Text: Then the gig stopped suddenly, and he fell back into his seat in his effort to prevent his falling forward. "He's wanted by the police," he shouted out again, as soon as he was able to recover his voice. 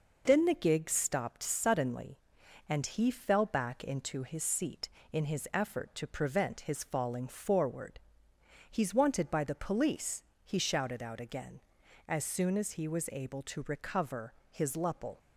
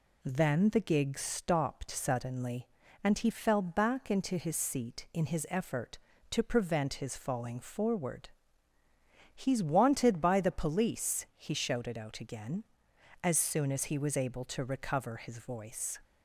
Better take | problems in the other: second | pauses between "recover" and "his"; slight; at 14.3 s; 0.16 s long // says "lupple" for "voice"; at 14.7 s

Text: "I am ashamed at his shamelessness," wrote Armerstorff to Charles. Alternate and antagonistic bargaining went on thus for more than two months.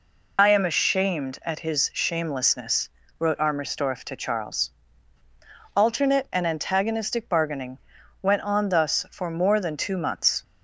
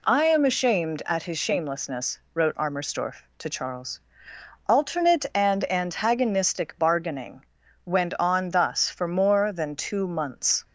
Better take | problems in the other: second | loses the start of "I"; at 0.3 s; 30 ms // pauses between "bargaining" and "went"; at 7.7 s; 0.42 s long; also in the second

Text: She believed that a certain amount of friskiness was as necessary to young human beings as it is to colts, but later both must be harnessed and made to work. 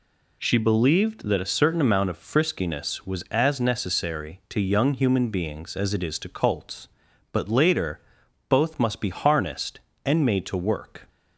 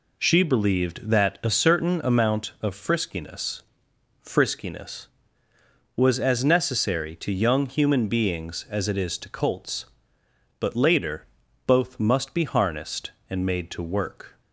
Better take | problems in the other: first | says "friskiness" twice; at 4.2 s // pauses between "later" and "both"; at 11.2 s; 0.44 s long; noticeable in the first

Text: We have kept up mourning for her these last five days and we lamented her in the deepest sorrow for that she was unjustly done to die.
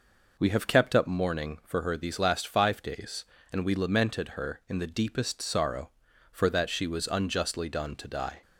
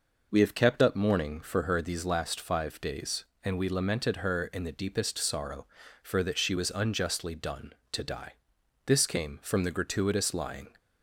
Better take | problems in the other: first | goes on to say "This came from the gratuitous lying"; strong; from 8.8 s on; 1.8 s long

